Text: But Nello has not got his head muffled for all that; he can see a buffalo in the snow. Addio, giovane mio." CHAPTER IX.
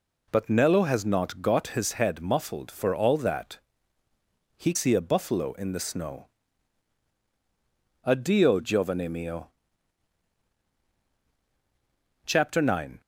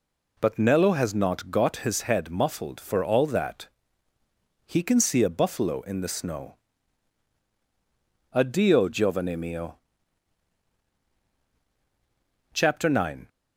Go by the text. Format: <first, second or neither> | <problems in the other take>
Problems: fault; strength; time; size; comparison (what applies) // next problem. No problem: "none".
second | skips "can"; at 4.7 s